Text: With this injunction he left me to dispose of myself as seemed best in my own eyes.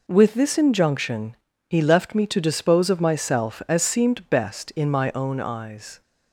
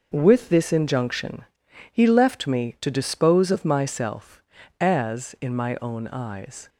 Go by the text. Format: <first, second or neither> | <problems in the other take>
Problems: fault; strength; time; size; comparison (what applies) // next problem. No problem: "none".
first | pauses between "injunction" and "he"; at 1.4 s; 0.44 s long; slight in the first // skips "seemed best"; at 5.3 s